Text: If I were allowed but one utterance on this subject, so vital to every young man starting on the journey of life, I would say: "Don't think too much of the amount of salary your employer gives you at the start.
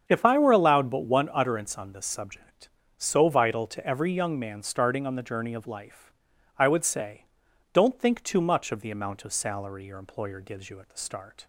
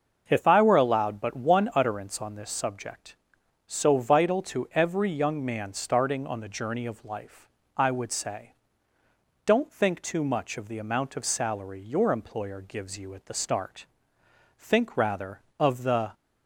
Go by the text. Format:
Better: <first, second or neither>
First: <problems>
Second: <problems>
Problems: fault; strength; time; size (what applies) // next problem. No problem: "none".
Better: first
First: starts louder than the rest; strong; until 1.0 s; 7.5 dB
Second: starts louder than the rest; until 1.2 s; 6.5 dB // goes on to say "Think rather of the"; from 14.5 s on; 1.5 s long